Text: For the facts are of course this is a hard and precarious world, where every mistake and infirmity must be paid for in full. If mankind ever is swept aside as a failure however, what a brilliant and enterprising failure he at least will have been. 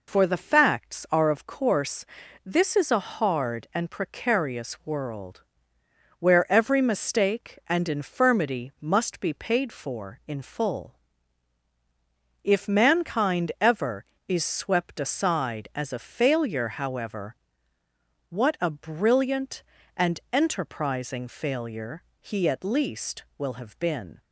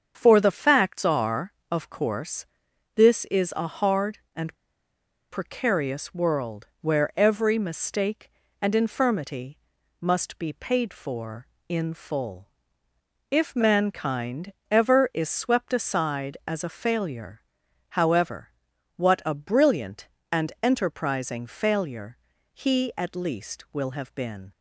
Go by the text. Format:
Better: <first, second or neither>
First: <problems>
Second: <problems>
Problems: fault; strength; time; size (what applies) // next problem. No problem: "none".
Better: first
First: pauses between "course" and "this"; at 2.0 s; 0.40 s long // pauses between "failure" and "he"; slight; at 22.0 s; 0.18 s long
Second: starts louder than the rest; strong; until 1.1 s; 7 dB // pauses between "course" and "this"; noticeable; at 2.4 s; 0.48 s long // pauses between "and" and "precarious"; noticeable; at 4.5 s; 0.75 s long // pauses between "infirmity" and "must"; at 9.5 s; 0.44 s long // pauses between "mankind" and "ever"; slight; at 14.5 s; 0.18 s long // pauses between "failure" and "however"; noticeable; at 17.4 s; 0.50 s long // pauses between "failure" and "he"; slight; at 22.1 s; 0.36 s long